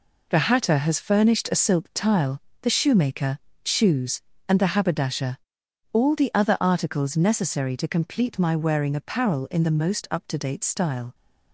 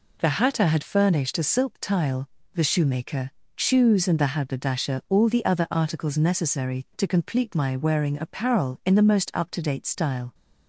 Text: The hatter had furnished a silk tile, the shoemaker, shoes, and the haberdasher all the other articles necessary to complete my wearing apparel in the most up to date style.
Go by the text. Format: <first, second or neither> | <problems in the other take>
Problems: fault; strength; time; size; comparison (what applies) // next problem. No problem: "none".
second | says "has" for "had"; at 0.7 s // pauses between "haberdasher" and "all"; noticeable; at 5.3 s; 0.54 s long